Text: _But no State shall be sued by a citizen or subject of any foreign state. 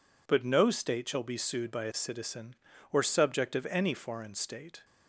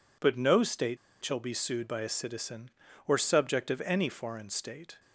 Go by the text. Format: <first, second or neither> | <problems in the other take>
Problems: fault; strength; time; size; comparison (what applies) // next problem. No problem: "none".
first | pauses between "State" and "shall"; slight; at 0.9 s; 0.28 s long